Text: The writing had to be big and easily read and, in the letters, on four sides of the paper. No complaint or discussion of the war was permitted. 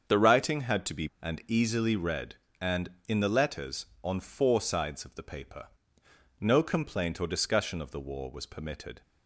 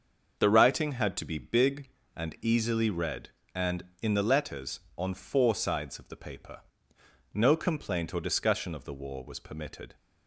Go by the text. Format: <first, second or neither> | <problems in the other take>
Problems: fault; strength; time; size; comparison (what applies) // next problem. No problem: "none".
second | starts louder than the rest; until 1.2 s; 7 dB; also in the second // skips "big"; at 1.1 s